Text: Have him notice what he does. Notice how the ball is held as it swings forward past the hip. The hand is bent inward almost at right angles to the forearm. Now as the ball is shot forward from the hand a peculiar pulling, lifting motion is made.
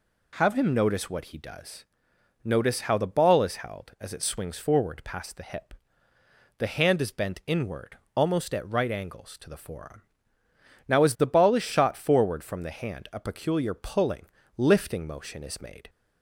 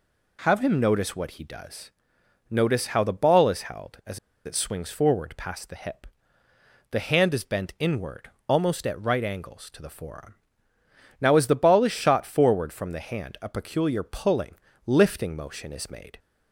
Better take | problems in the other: first | pauses between "as" and "it"; slight; at 4.1 s; 0.27 s long // pauses between "inward" and "almost"; slight; at 8.3 s; 0.18 s long; slight in the first

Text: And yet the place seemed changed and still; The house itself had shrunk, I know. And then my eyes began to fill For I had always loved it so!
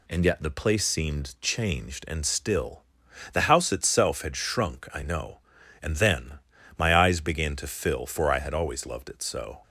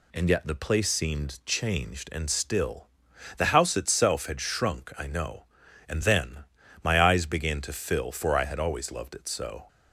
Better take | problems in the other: neither | pauses between "then" and "my"; slight; the same in both

